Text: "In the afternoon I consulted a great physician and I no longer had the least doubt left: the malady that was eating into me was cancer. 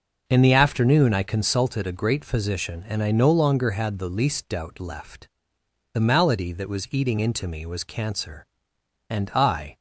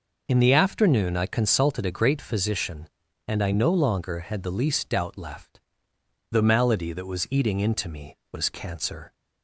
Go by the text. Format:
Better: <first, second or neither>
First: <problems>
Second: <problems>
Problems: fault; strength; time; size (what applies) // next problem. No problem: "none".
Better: second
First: goes on to say "And I"; noticeable; from 9.0 s on; 0.66 s long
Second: none